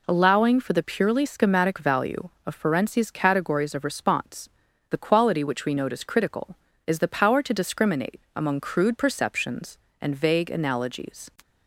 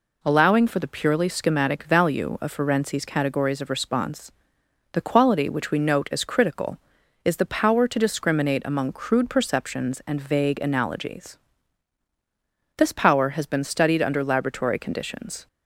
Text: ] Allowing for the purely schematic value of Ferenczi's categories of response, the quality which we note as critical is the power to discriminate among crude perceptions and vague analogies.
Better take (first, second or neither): first